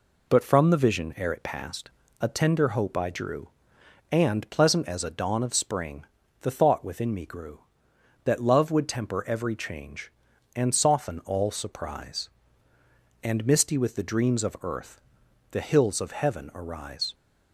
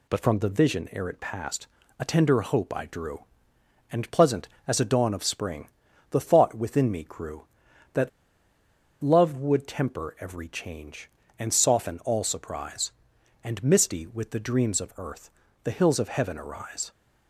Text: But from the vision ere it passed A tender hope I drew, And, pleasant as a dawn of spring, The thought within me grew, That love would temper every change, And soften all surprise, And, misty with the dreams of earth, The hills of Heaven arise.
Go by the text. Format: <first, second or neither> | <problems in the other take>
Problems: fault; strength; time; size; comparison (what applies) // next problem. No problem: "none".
first | pauses between "passed" and "A"; slight; at 1.6 s; 0.32 s long; slight in the first // pauses between "That" and "love"; noticeable; at 8.0 s; 0.92 s long